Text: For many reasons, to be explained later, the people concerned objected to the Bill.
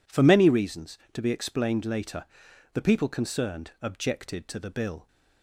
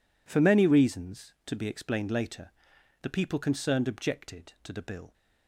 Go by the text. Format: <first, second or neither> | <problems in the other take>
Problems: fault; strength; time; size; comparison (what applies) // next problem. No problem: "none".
neither | none